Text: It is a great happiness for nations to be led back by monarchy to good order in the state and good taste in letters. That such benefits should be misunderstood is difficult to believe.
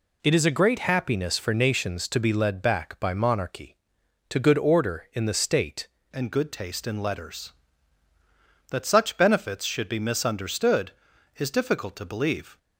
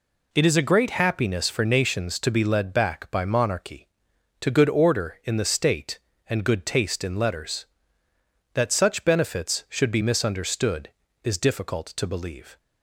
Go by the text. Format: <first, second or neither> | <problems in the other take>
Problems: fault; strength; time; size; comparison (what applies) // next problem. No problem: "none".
second | changes voice at "and"; from 6.1 s on; 6.4 s long